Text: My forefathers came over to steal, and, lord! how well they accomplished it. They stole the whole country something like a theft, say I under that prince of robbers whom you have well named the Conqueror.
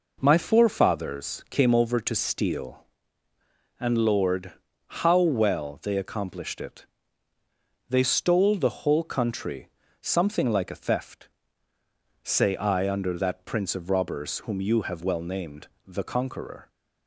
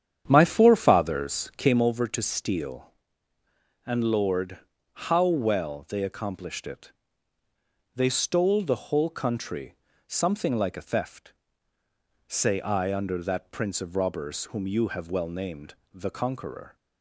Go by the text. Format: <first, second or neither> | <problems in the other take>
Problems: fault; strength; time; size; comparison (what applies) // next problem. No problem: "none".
first | starts louder than the rest; strong; until 1.8 s; 9 dB // pauses between "country" and "something"; slight; at 9.7 s; 0.34 s long; slight in the first // pauses between "named" and "the"; slight; at 15.7 s; 0.18 s long; slight in the first